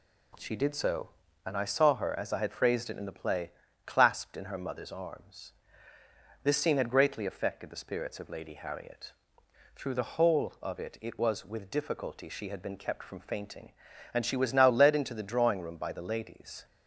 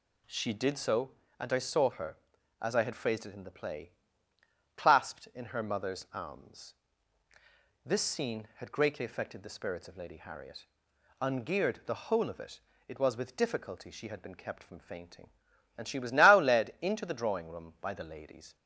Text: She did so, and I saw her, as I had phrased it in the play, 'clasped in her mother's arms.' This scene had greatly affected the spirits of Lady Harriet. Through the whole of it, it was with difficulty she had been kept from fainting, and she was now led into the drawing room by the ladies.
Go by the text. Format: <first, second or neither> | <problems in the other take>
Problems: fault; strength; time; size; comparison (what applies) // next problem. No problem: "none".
first | says "Ungeared" for "Through"; at 11.1 s